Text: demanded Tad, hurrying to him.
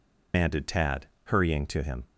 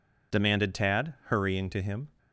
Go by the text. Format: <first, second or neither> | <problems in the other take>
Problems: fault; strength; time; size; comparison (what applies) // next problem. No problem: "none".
second | loses the start of "demanded"; at 0.3 s; 145 ms